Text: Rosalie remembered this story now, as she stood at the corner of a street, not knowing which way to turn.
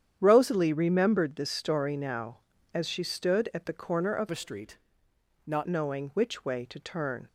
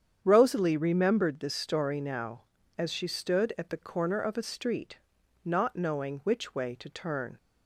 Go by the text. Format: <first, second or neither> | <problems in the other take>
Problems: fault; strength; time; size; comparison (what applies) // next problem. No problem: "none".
second | starts louder than the rest; strong; until 1.2 s; 9 dB; strong in the second // changes voice from "a" to "not"; from 4.3 to 5.6 s; 1.3 s long